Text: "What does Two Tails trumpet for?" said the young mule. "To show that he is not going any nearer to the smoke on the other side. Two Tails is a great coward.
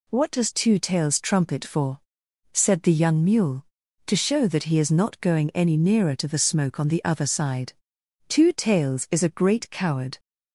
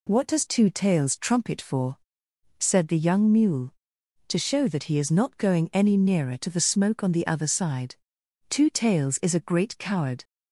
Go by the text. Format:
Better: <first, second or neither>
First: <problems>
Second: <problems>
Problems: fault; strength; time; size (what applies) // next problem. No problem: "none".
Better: neither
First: none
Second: none